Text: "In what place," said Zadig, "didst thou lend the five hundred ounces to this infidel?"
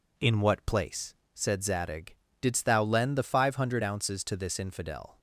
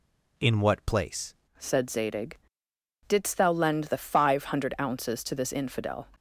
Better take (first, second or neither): first